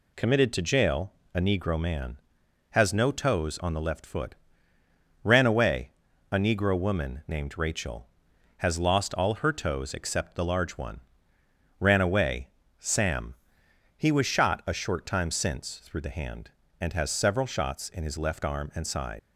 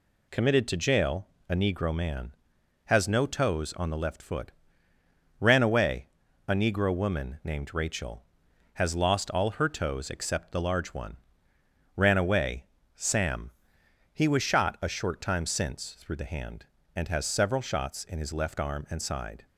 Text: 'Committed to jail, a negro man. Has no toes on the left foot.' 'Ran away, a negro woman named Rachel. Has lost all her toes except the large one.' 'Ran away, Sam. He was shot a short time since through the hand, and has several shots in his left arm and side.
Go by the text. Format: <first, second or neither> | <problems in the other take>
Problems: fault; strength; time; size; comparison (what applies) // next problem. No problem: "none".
second | leaves "side" unfinished; at 19.1 s; 125 ms